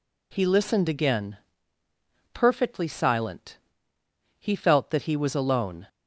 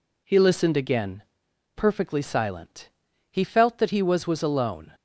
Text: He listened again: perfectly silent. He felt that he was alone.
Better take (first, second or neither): first